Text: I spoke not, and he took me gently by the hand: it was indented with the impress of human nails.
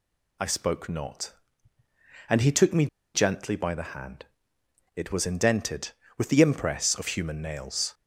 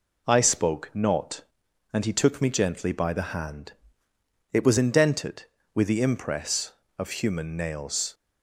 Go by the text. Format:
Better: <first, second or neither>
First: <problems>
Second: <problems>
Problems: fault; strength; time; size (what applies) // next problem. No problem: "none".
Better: second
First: pauses between "me" and "gently"; slight; at 2.8 s; 0.28 s long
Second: none